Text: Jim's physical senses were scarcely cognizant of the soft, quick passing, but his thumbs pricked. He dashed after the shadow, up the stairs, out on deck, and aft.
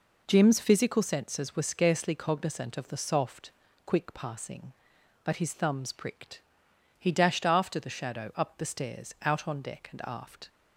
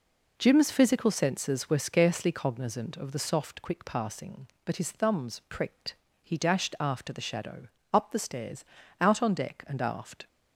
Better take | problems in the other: neither | none

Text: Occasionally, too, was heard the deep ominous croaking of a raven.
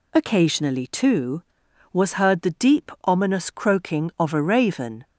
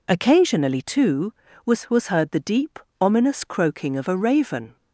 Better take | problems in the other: first | says "was" twice; at 1.9 s // pauses between "deep" and "ominous"; slight; at 2.7 s; 0.20 s long

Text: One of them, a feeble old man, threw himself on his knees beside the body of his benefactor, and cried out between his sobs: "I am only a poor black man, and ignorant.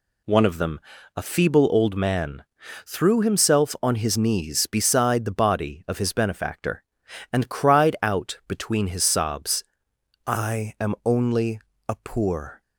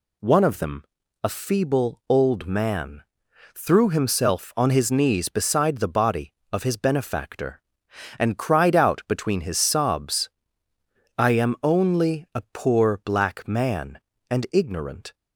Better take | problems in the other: second | pauses between "only" and "a"; slight; at 11.5 s; 0.30 s long // stops before "black man and ignorant"; at 12.6 s

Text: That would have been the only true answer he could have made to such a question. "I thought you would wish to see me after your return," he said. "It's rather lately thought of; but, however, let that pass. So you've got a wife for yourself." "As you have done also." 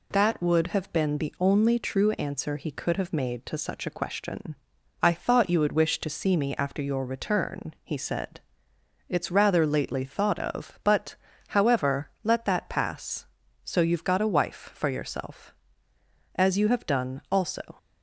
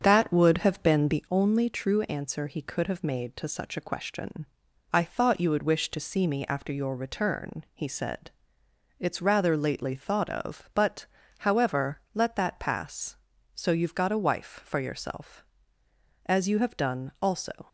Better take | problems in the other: first | starts louder than the rest; strong; until 1.3 s; 7.5 dB

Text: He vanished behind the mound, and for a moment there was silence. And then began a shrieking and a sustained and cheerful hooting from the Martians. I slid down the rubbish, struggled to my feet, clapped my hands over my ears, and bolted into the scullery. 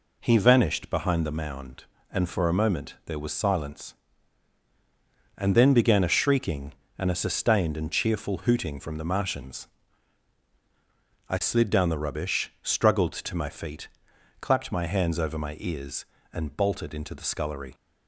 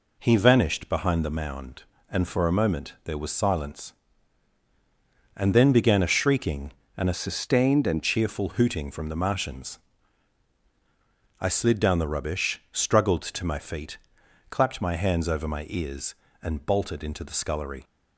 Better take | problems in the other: first | changes voice from "sustained" to "and"; from 7.1 to 8.0 s; 0.9 s long

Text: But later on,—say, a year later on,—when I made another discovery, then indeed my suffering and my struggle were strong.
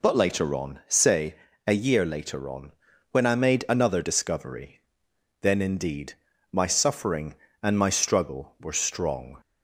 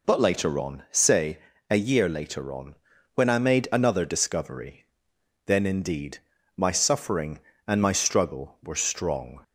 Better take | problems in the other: neither | pauses between "indeed" and "my"; the same in both

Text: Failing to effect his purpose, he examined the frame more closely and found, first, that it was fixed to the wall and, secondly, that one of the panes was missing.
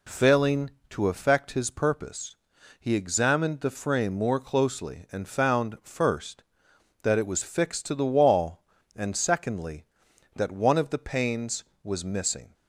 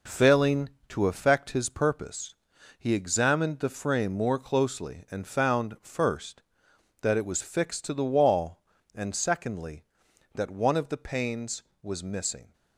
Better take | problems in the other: first | gets quieter; throughout; 6 dB

